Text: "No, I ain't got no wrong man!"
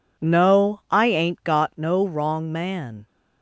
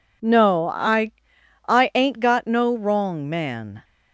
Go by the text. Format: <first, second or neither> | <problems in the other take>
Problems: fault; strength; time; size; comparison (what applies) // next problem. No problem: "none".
first | says "I" twice; at 1.6 s